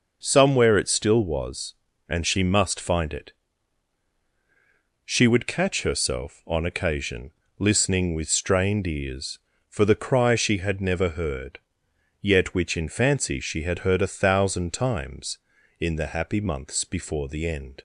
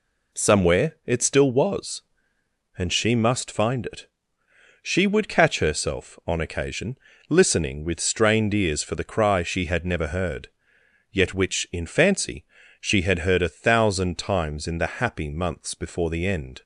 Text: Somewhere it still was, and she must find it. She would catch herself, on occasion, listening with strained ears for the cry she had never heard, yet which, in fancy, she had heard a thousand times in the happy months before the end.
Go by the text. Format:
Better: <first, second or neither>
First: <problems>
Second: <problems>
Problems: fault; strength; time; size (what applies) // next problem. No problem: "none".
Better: neither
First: none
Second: none